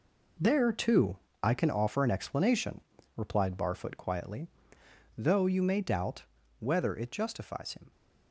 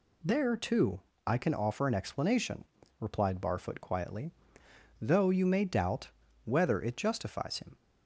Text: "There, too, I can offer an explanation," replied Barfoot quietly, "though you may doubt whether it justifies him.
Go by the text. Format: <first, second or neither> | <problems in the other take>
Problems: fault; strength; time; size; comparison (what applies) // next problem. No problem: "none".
second | gets quieter; strong; throughout; 10.5 dB // pauses between "doubt" and "whether"; slight; at 6.2 s; 0.32 s long; slight in the second